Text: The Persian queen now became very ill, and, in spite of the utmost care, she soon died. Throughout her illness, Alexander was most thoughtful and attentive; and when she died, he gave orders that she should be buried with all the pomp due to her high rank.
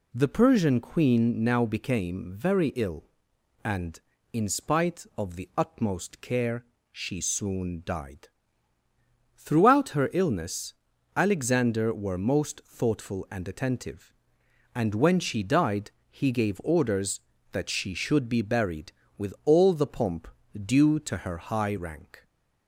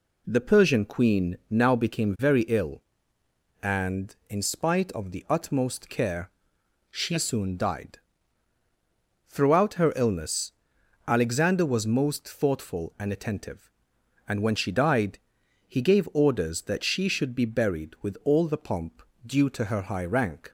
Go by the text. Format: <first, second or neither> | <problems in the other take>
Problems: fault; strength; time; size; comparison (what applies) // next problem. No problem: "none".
second | says "were" for "was"; at 11.9 s // pauses between "pomp" and "due"; slight; at 20.2 s; 0.26 s long; slight in the second